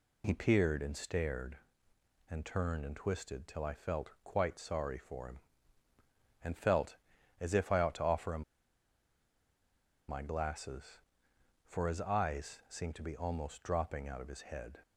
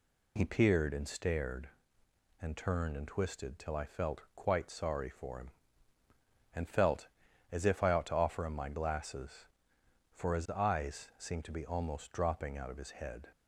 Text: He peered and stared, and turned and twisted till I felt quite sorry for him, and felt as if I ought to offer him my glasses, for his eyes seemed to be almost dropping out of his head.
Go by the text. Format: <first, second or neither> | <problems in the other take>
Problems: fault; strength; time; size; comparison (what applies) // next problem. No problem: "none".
second | pauses between "him" and "my"; strong; at 8.4 s; 1.6 s long